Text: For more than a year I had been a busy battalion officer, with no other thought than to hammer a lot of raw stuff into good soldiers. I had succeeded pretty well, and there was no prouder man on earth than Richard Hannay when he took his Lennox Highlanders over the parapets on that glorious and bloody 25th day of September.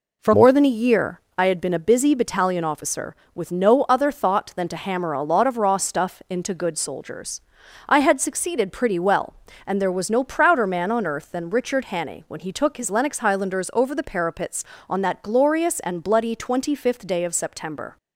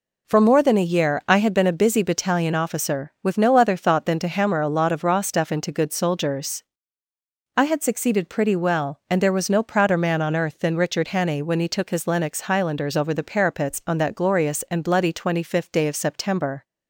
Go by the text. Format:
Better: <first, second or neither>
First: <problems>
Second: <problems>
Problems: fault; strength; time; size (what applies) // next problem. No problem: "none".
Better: second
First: changes voice at "more"; from 0.3 s on; 17.6 s long // pauses between "year" and "I"; slight; at 1.2 s; 0.16 s long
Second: none